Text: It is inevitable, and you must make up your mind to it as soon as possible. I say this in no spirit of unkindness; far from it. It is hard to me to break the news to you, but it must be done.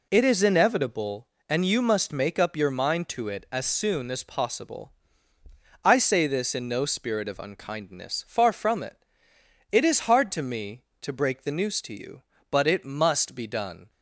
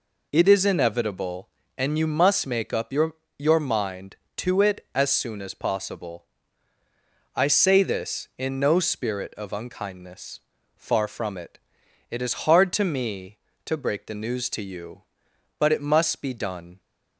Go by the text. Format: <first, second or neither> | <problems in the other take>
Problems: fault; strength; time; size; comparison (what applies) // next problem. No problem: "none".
first | says "your" twice; at 3.3 s